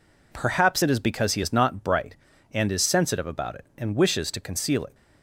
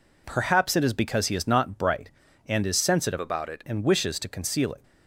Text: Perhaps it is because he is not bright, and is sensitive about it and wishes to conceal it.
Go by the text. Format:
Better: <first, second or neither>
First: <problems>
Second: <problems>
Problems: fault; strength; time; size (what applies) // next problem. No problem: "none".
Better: first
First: none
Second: changes voice from "about" to "it"; from 3.2 to 3.6 s; 0.4 s long